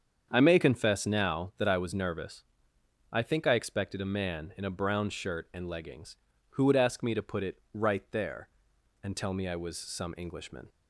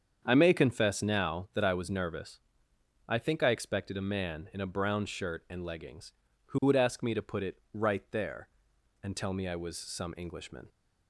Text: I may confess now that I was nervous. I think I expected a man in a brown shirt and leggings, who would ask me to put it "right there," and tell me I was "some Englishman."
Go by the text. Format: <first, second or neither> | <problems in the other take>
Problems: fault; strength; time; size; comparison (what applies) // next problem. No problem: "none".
neither | starts louder than the rest; strong; the same in both